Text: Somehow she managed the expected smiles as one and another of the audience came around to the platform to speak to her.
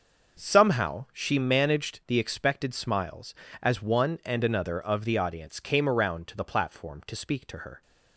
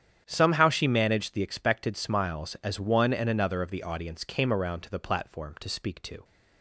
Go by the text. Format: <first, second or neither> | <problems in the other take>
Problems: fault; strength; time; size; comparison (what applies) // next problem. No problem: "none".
first | starts louder than the rest; strong; until 1.2 s; 9 dB; noticeable in the first // stops before "her"; at 6.2 s